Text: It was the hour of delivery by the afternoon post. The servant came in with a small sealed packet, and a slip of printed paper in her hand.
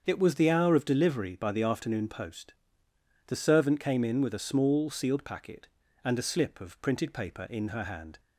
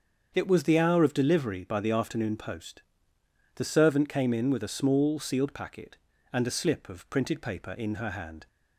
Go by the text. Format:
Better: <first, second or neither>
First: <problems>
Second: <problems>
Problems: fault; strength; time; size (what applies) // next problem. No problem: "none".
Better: neither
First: starts louder than the rest; until 1.0 s; 7 dB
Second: starts louder than the rest; until 1.3 s; 7 dB